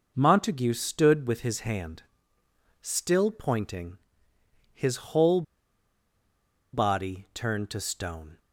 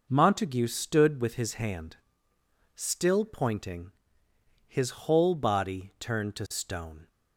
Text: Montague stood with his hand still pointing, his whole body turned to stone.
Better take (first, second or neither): second